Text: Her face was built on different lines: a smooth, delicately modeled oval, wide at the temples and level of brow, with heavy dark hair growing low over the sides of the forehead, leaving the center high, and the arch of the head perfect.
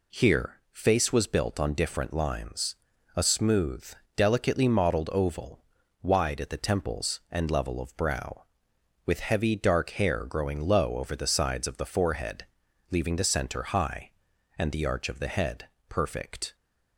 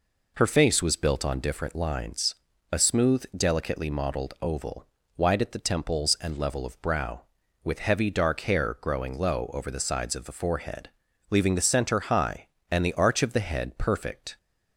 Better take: second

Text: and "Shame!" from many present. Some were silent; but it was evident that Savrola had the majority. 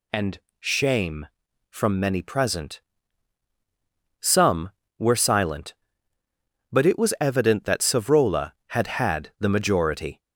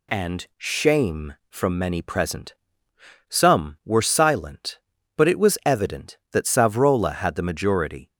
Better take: second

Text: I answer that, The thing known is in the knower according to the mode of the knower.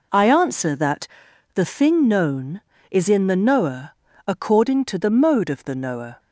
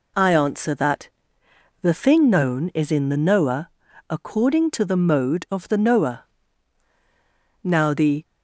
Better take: first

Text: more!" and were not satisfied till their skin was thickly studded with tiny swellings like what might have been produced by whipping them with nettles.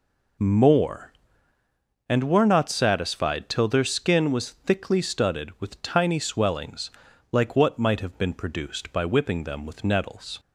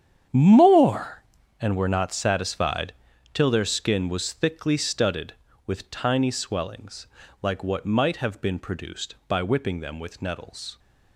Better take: first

